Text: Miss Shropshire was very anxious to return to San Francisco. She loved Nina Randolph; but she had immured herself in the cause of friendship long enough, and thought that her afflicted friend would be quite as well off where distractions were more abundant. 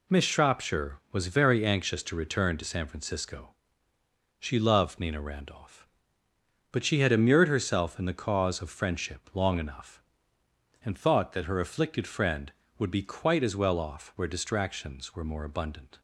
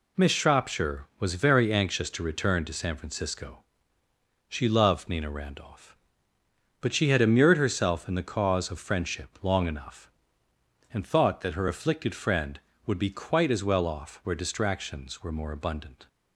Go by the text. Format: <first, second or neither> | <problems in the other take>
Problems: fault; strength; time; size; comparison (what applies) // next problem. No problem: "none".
neither | none